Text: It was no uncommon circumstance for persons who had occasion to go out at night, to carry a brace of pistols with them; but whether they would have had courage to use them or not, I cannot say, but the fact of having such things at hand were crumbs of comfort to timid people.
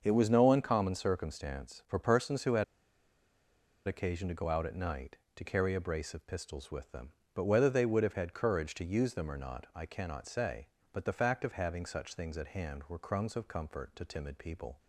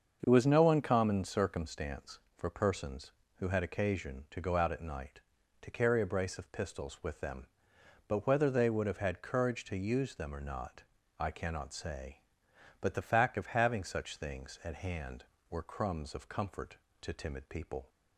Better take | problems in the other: second | starts louder than the rest; until 1.0 s; 6.5 dB; also in the second // pauses between "had" and "occasion"; at 2.6 s; 1.2 s long

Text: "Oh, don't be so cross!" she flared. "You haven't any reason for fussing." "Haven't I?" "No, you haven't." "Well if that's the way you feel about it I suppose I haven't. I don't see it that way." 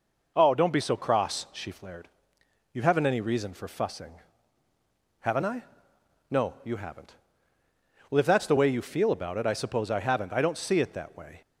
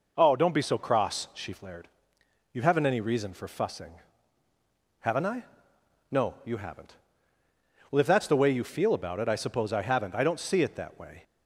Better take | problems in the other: neither | none

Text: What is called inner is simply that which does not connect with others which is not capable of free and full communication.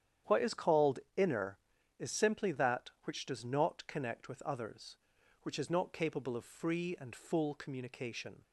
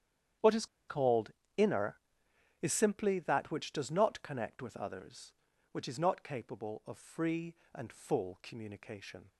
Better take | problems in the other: first | starts louder than the rest; strong; until 1.8 s; 9.5 dB; strong in the first // pauses between "is" and "called"; slight; at 0.6 s; 0.23 s long // pauses between "called" and "inner"; slight; at 1.3 s; 0.24 s long; slight in the first

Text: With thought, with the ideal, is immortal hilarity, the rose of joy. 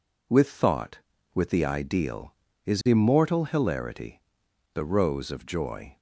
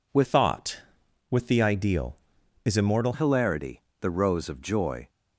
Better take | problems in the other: first | changes voice from "thought" to "immortal"; from 0.2 to 3.1 s; 2.9 s long

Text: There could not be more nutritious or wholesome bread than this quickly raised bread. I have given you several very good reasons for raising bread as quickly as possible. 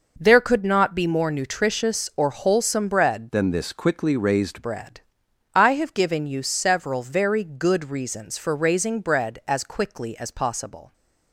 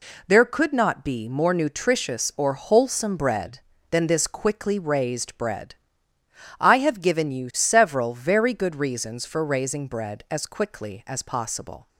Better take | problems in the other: second | changes voice from "than" to "raised"; from 3.3 to 4.6 s; 1.3 s long

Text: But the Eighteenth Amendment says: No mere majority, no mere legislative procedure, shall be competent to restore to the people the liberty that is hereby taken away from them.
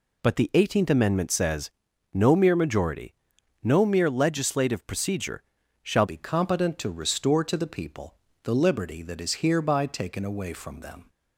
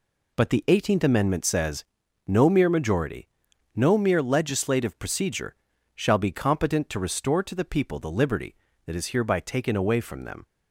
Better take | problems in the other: second | changes voice at "be"; from 6.0 s on; 5.0 s long // pauses between "people" and "the"; slight; at 8.1 s; 0.28 s long

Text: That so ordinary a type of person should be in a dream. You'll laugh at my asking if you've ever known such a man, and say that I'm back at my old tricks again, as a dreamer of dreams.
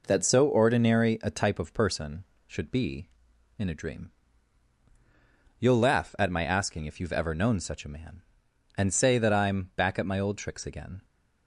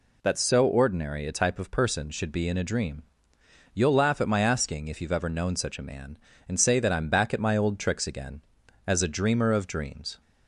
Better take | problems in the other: second | stops before "as a dreamer of dreams"; at 11.0 s

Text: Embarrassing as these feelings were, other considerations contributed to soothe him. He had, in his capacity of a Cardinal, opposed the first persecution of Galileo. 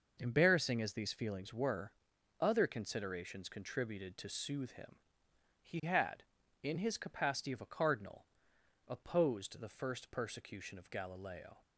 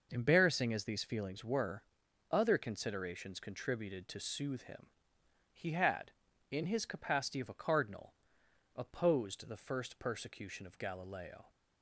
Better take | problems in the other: neither | none

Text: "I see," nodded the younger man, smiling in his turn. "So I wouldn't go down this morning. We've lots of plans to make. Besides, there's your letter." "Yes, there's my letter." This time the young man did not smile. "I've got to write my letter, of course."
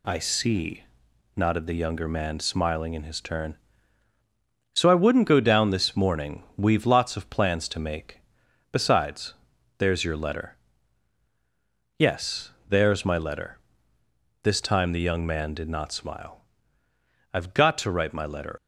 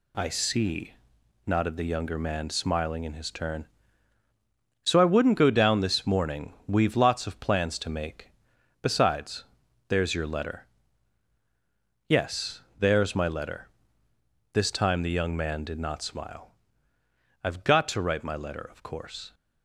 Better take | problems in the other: second | stops before "of course"; at 18.5 s

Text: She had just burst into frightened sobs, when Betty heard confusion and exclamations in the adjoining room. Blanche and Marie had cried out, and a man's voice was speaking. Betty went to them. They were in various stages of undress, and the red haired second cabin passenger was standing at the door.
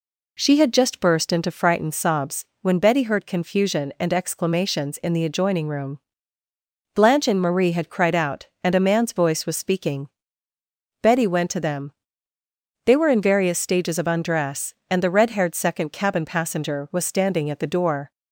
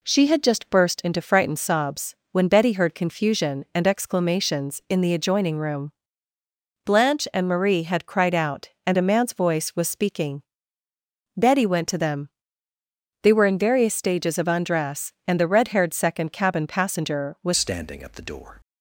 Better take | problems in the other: first | changes voice at "standing"; from 17.5 s on; 1.1 s long

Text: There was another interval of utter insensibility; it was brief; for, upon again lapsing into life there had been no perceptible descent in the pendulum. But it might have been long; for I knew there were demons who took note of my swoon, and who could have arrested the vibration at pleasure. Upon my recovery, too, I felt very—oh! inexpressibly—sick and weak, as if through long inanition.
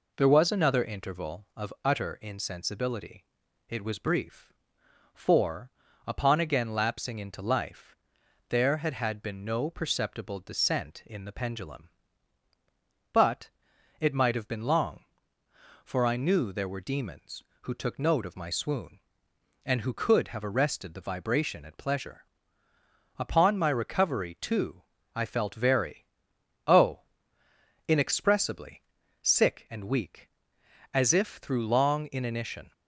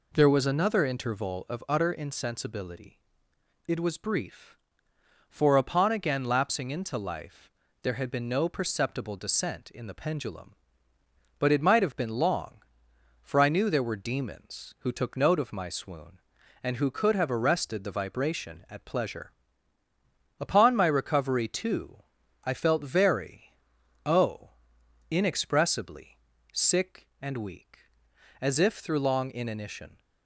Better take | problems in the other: second | pauses between "life" and "there"; noticeable; at 7.9 s; 0.54 s long; slight in the second // says "had" twice; at 8.9 s // pauses between "But" and "it"; noticeable; at 13.4 s; 0.50 s long

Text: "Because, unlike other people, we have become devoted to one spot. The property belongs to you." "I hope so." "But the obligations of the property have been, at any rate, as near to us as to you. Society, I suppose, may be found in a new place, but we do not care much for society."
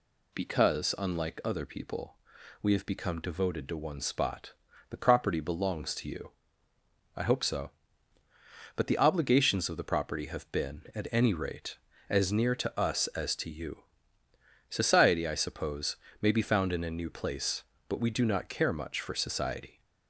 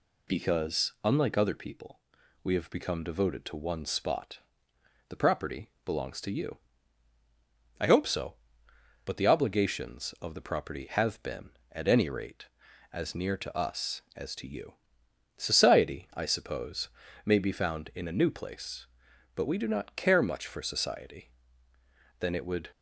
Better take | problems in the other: first | pauses between "property" and "belongs"; slight; at 5.7 s; 0.16 s long // goes on to say "Then it would"; from 22.1 s on; 0.50 s long

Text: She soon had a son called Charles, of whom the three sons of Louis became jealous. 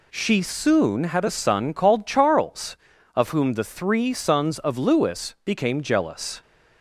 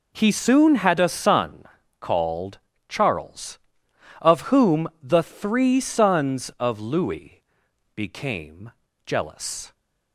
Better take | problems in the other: first | says "He" for "She"; at 0.1 s // pauses between "son" and "called"; slight; at 1.6 s; 0.36 s long // pauses between "called" and "Charles"; slight; at 2.5 s; 0.28 s long // pauses between "Louis" and "became"; noticeable; at 7.4 s; 0.54 s long // pauses between "became" and "jealous"; at 8.6 s; 0.38 s long

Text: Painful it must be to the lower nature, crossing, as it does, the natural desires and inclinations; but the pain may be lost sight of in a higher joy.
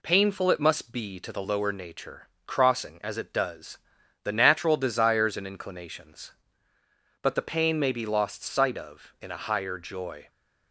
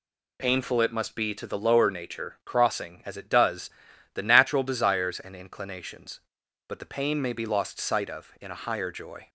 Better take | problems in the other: neither | none

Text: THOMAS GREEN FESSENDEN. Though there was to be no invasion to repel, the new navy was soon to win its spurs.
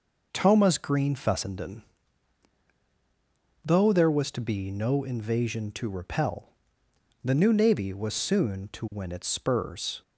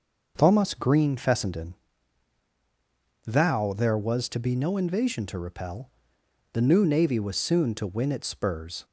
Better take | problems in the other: first | says "Thou" for "Though"; at 3.2 s

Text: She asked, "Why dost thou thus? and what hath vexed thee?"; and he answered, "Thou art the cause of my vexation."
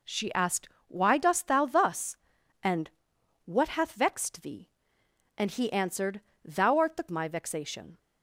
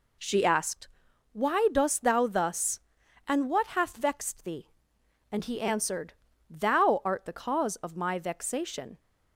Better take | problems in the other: second | pauses between "and" and "what"; noticeable; at 2.9 s; 0.56 s long // skips "cause of"; at 7.0 s

